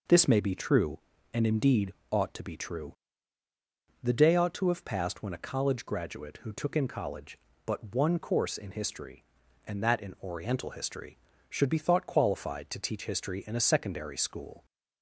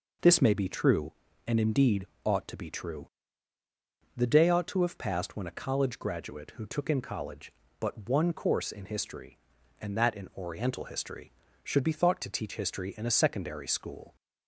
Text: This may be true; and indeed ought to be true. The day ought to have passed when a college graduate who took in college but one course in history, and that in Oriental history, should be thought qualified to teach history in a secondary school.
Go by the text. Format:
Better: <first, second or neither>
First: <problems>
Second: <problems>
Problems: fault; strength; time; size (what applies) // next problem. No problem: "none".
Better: first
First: pauses between "indeed" and "ought"; slight; at 1.9 s; 0.20 s long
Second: pauses between "indeed" and "ought"; slight; at 2.0 s; 0.20 s long // skips "qualified"; at 12.1 s